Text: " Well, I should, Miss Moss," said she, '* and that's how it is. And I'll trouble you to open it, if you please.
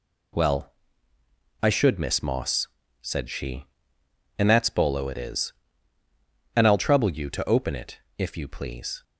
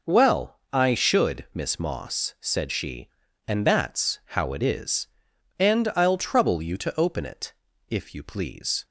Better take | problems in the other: second | says "bolo" for "how"; at 4.6 s

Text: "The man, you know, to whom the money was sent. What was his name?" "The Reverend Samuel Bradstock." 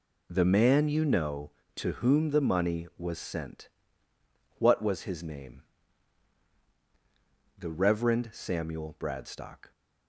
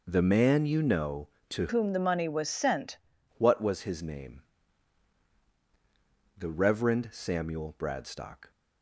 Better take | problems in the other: first | changes voice from "whom" to "sent"; from 1.6 to 2.9 s; 1.3 s long

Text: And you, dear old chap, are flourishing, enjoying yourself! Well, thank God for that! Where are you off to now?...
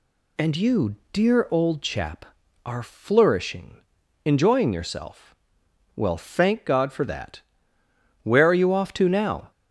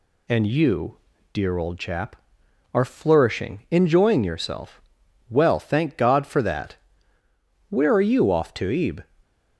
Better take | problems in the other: first | says "ebe" for "now"; at 8.6 s

